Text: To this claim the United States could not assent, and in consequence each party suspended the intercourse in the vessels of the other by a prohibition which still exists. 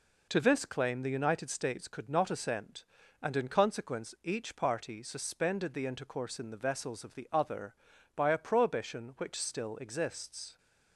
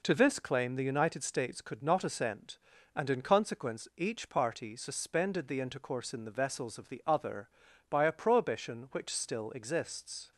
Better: neither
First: none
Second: none

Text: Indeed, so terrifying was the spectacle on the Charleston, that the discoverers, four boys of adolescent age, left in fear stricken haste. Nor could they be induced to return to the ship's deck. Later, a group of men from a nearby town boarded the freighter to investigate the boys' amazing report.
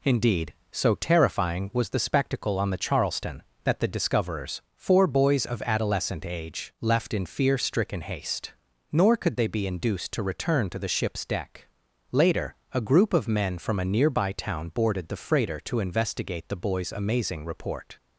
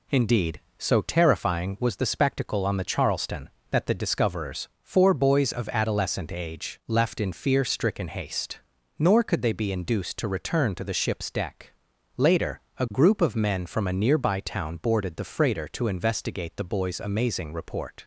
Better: neither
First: none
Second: none

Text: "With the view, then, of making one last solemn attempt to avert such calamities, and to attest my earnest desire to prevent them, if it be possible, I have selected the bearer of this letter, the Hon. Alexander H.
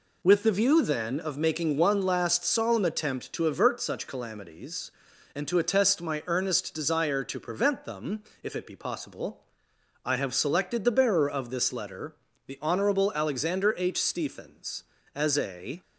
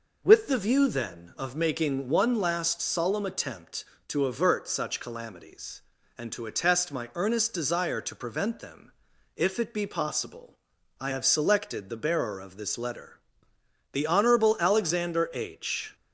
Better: second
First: goes on to say "Stephens as a"; strong; from 13.9 s on; 1.8 s long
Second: none

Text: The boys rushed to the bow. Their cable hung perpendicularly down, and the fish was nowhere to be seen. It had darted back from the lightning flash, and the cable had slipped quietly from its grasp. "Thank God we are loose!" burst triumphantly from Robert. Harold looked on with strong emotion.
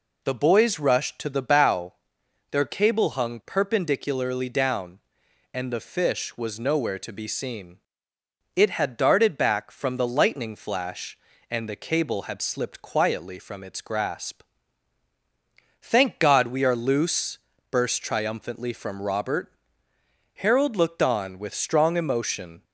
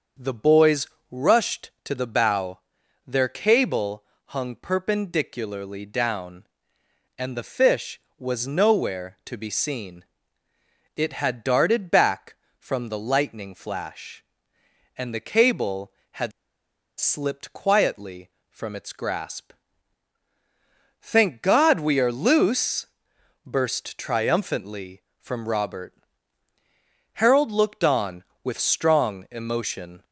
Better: first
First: none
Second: starts louder than the rest; until 1.4 s; 6.5 dB // pauses between "boys" and "rushed"; slight; at 0.8 s; 0.24 s long // pauses between "cable" and "hung"; slight; at 4.0 s; 0.28 s long // pauses between "had" and "slipped"; noticeable; at 16.3 s; 0.67 s long

